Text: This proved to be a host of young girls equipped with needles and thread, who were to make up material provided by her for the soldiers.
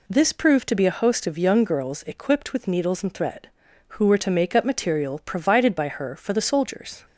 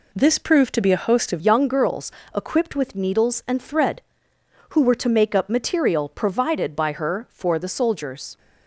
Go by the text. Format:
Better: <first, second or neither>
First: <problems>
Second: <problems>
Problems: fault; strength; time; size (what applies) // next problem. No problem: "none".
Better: first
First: none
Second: changes voice at "young"; from 1.3 s on; 7.0 s long // pauses between "girls" and "equipped"; slight; at 2.1 s; 0.22 s long